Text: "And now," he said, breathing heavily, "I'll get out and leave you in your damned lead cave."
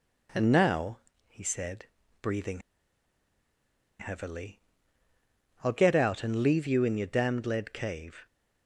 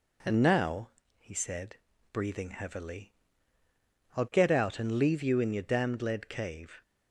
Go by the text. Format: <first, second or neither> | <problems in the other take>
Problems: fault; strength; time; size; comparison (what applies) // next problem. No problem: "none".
second | pauses between "breathing" and "heavily"; strong; at 2.6 s; 1.3 s long